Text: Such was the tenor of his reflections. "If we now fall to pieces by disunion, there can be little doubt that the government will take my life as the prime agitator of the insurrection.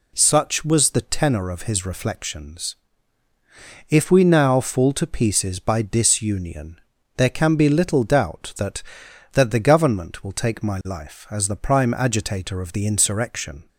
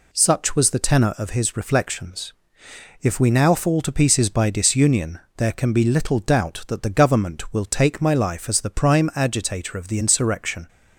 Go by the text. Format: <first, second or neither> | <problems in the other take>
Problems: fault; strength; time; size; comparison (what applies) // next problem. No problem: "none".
second | says "that" twice; at 9.3 s